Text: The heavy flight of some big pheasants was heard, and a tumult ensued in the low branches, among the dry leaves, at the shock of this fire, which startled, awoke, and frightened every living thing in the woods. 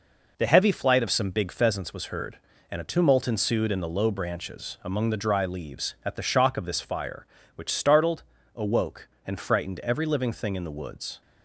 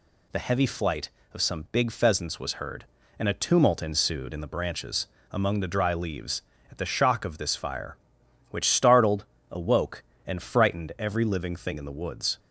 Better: first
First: none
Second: skips "low"; at 4.4 s

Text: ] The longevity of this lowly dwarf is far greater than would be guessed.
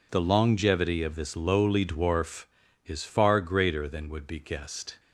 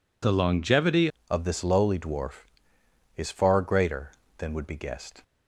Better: first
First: none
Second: changes voice at "of"; from 1.3 s on; 3.9 s long

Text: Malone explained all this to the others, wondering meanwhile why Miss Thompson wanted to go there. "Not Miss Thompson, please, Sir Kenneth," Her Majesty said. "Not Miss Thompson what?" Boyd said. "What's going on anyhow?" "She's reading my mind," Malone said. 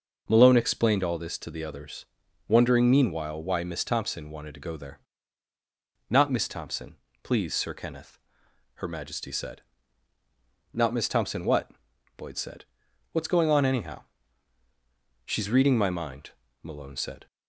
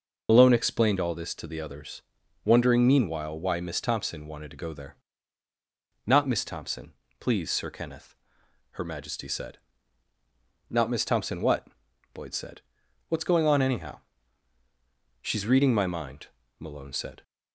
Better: first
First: none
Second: loses the start of "Malone"; at 0.2 s; 45 ms

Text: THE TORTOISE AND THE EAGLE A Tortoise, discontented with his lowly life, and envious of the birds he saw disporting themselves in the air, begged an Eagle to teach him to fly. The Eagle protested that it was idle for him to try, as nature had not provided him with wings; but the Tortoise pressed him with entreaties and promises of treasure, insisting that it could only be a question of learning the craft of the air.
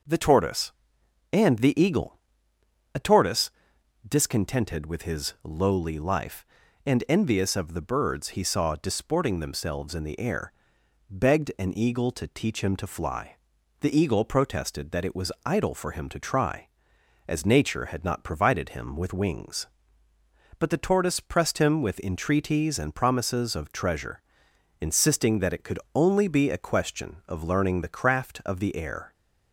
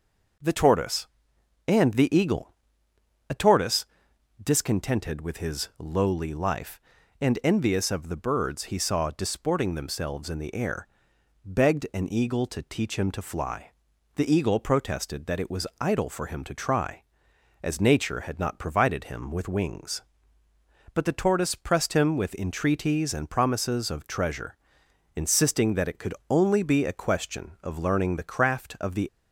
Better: first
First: pauses between "EAGLE" and "A"; noticeable; at 2.1 s; 0.74 s long // pauses between "could" and "only"; slight; at 25.7 s; 0.16 s long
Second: pauses between "EAGLE" and "A"; noticeable; at 2.5 s; 0.74 s long // pauses between "could" and "only"; slight; at 26.1 s; 0.16 s long // stops before "air"; at 29.0 s

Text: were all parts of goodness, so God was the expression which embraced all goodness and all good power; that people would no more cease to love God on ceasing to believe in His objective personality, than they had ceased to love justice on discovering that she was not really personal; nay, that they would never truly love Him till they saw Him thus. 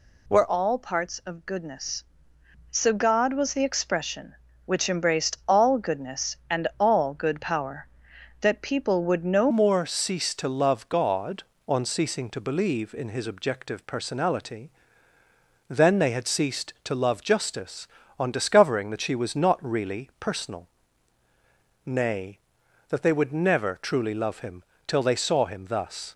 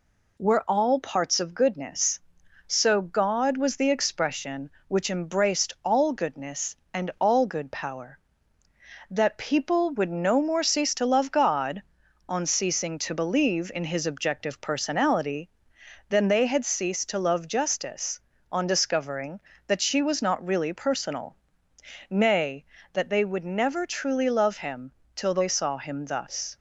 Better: second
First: changes voice at "more"; from 9.4 s on; 16.7 s long // pauses between "Him" and "till"; slight; at 24.6 s; 0.24 s long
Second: pauses between "Him" and "till"; slight; at 24.9 s; 0.24 s long

